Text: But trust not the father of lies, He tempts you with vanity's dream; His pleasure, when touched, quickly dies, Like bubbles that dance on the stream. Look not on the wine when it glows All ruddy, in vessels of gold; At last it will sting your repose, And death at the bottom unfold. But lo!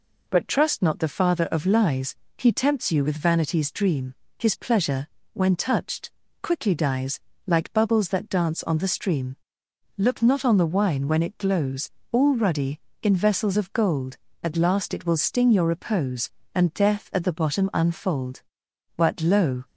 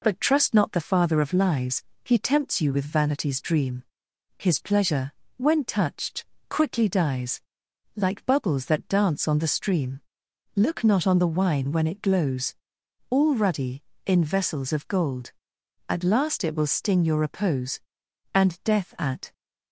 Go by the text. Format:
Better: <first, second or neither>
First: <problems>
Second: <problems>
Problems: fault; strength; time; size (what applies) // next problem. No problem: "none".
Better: first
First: pauses between "glows" and "All"; slight; at 11.9 s; 0.20 s long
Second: pauses between "glows" and "All"; noticeable; at 12.5 s; 0.56 s long // stops before "the bottom unfold But lo"; at 19.3 s